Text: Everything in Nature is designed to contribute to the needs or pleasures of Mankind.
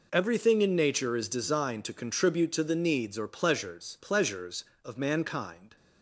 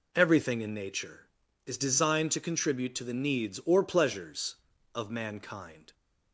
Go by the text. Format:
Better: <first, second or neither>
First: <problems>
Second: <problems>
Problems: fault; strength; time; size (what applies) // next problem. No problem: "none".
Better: second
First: says "pleasures" twice; at 4.0 s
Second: none